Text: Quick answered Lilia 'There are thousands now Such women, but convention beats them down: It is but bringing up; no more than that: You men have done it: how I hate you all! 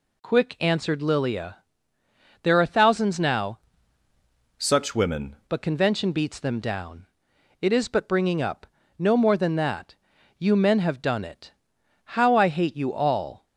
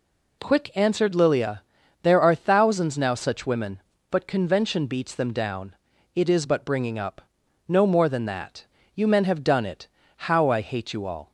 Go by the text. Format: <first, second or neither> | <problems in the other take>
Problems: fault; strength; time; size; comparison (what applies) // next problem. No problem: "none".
second | pauses between "Lilia" and "There"; noticeable; at 1.5 s; 0.84 s long; also in the second // changes voice from "Such" to "women"; from 4.5 to 5.3 s; 0.8 s long